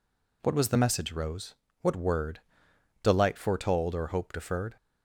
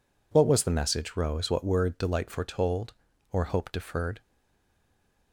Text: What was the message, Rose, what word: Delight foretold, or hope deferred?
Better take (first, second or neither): first